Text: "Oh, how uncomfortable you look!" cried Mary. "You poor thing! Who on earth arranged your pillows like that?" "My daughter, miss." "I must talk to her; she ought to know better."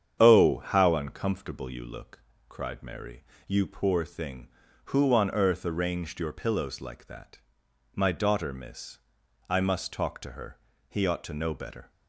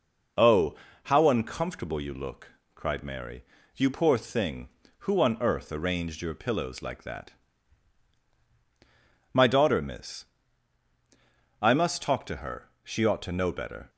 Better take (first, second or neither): second